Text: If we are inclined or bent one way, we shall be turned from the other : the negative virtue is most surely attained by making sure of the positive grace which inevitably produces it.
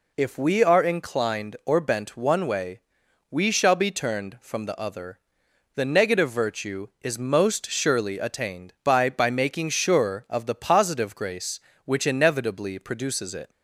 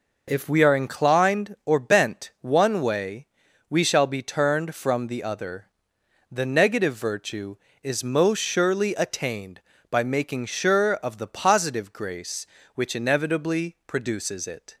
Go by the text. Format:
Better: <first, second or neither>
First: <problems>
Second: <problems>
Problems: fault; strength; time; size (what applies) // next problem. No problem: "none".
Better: second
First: says "by" twice; at 9.0 s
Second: none